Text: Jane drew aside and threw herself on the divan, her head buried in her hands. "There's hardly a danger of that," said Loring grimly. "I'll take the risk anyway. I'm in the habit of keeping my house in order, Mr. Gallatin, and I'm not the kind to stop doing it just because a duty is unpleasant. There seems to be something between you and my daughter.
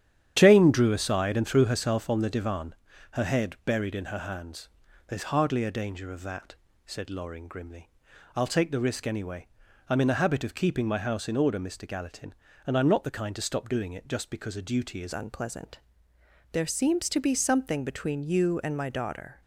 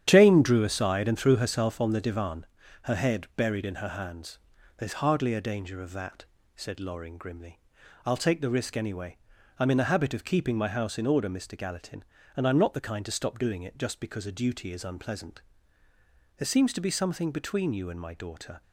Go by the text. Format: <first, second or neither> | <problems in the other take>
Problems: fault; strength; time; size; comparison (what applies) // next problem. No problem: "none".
second | starts louder than the rest; strong; until 1.3 s; 9.5 dB; strong in the second // changes voice at "unpleasant"; from 15.1 s on; 4.3 s long